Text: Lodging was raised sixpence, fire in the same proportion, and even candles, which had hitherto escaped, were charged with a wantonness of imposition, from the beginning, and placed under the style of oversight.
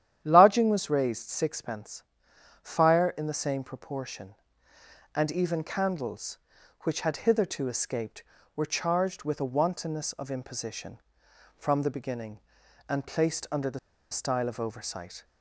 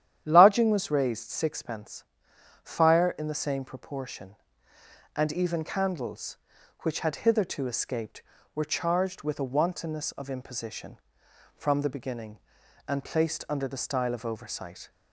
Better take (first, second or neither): second